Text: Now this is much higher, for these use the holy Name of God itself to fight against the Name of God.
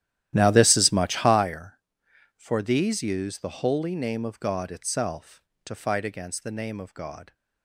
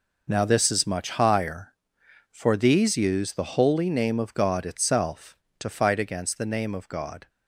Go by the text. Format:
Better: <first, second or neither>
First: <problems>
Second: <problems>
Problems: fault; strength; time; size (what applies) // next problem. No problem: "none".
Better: second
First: starts louder than the rest; strong; until 1.5 s; 12.5 dB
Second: none